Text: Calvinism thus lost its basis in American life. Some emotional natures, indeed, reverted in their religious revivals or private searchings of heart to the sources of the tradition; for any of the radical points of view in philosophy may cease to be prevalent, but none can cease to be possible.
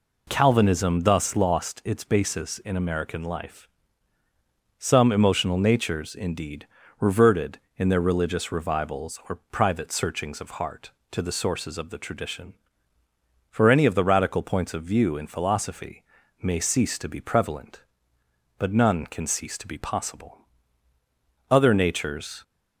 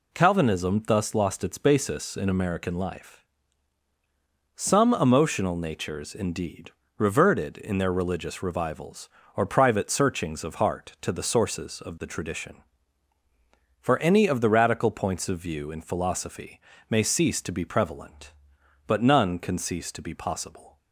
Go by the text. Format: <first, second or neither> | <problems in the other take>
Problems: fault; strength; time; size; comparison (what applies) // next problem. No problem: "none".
second | pauses between "philosophy" and "may"; at 16.0 s; 0.40 s long; slight in the second // goes on to say "Other natures"; noticeable; from 21.4 s on; 0.94 s long